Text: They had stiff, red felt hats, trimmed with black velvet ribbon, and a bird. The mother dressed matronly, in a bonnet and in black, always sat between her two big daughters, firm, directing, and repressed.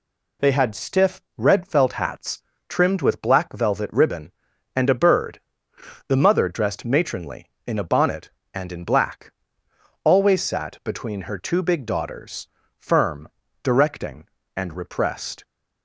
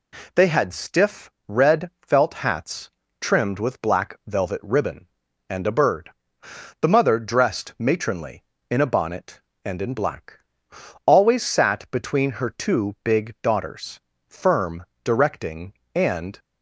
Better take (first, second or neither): first